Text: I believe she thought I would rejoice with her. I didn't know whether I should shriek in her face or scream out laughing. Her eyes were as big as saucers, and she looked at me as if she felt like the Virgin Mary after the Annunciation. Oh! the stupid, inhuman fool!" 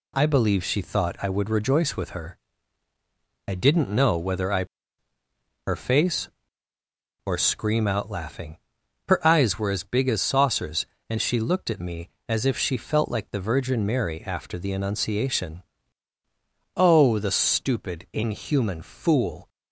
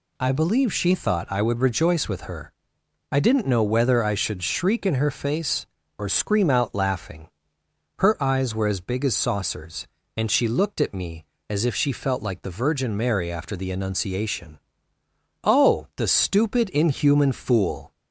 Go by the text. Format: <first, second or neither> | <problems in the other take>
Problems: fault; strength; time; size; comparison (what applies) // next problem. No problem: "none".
second | skips "should shriek in"; at 5.1 s